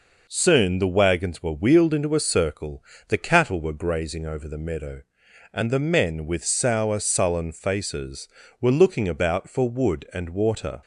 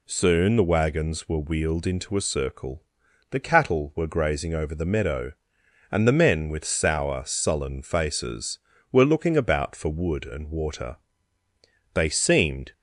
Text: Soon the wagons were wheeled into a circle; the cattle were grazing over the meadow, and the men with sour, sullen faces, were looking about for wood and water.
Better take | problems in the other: first | goes on to say "They seemed"; noticeable; from 11.9 s on; 0.78 s long

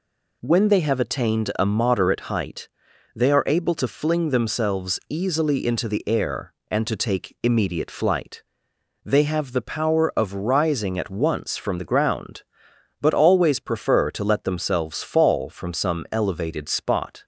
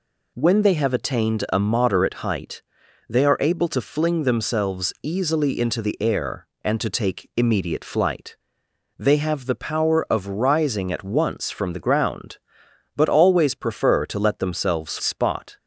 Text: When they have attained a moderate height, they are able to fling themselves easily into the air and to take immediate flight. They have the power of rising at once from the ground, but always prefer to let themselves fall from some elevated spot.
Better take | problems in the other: first | skips "fall from some elevated"; at 14.9 s

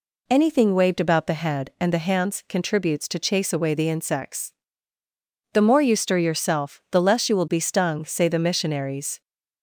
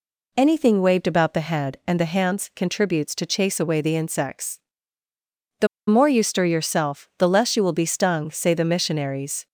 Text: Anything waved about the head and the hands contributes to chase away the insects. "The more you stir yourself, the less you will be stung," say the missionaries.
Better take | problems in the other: first | pauses between "The" and "more"; slight; at 5.6 s; 0.21 s long

